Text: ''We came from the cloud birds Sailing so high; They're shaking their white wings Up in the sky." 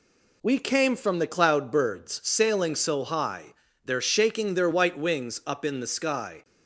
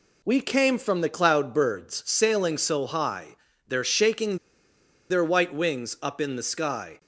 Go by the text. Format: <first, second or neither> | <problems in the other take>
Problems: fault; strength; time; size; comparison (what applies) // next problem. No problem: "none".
first | pauses between "shaking" and "their"; noticeable; at 4.3 s; 0.73 s long